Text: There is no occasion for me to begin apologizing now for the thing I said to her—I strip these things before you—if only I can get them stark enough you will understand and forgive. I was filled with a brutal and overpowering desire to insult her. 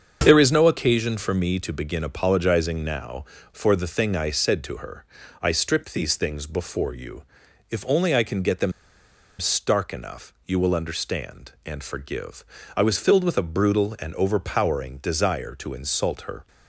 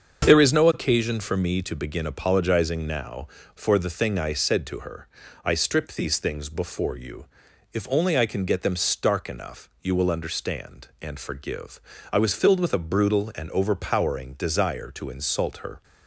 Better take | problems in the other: second | starts louder than the rest; until 1.2 s; 7 dB; also in the second // pauses between "them" and "stark"; noticeable; at 8.7 s; 0.66 s long

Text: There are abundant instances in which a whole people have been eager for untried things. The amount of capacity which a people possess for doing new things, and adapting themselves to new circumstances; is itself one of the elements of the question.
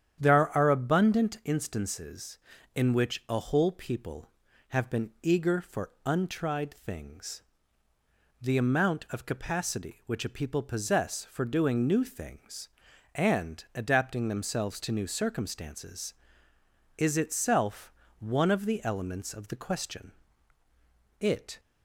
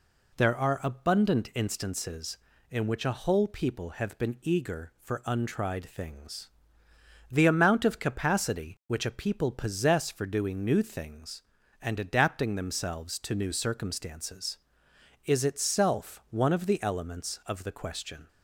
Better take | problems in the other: second | starts louder than the rest; strong; until 1.2 s; 9.5 dB // pauses between "itself" and "one"; slight; at 17.9 s; 0.24 s long // goes on to say "It"; slight; from 21.1 s on; 0.40 s long

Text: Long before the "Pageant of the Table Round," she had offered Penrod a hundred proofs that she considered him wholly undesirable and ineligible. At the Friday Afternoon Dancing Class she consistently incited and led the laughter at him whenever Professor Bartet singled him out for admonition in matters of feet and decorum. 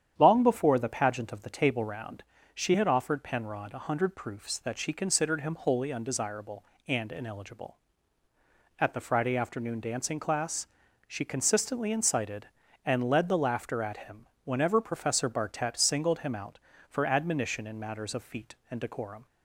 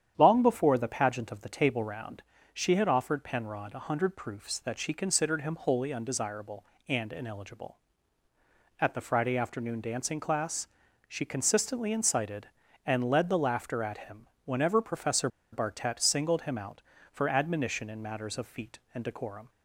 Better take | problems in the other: first | starts louder than the rest; strong; until 1.1 s; 9.5 dB; strong in the first // pauses between "Class" and "she"; at 10.6 s; 0.40 s long; also in the first // pauses between "him" and "whenever"; slight; at 14.2 s; 0.18 s long; slight in the first // pauses between "Professor" and "Bartet"; slight; at 15.2 s; 0.23 s long

